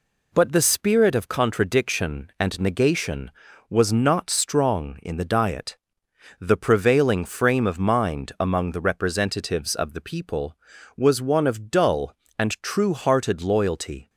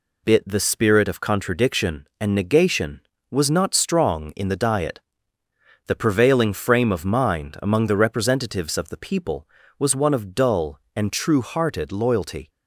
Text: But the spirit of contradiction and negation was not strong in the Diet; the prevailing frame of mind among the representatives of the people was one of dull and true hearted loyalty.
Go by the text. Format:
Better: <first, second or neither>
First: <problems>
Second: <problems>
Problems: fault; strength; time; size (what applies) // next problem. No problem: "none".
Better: first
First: none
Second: says "Bit" for "But"; at 0.2 s